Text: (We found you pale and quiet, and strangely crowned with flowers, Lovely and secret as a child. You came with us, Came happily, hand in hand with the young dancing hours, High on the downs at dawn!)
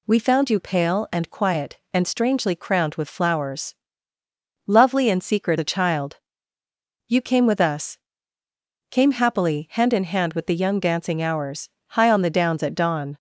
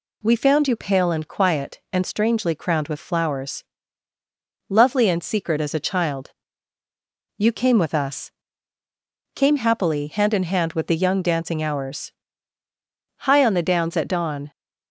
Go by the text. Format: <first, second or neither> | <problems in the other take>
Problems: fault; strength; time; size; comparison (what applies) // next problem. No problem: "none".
second | skips "as"; at 5.5 s